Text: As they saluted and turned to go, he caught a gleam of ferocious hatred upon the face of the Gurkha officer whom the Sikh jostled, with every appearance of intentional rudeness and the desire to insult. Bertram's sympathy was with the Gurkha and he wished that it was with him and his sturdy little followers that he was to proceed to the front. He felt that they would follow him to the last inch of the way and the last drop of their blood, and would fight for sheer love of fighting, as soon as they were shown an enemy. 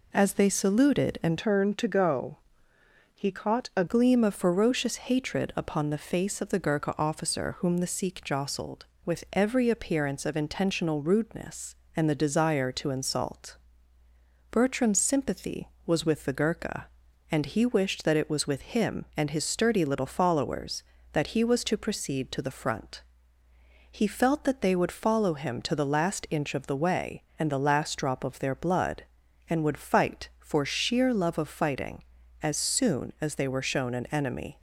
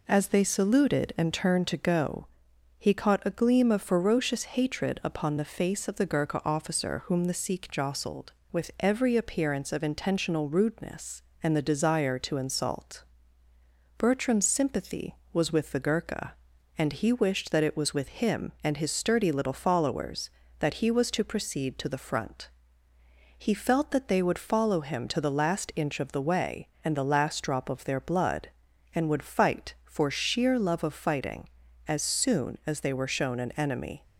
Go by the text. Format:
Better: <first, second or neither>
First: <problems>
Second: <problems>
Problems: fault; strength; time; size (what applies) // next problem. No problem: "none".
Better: second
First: changes voice from "turned" to "a"; from 1.3 to 3.8 s; 2.5 s long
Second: none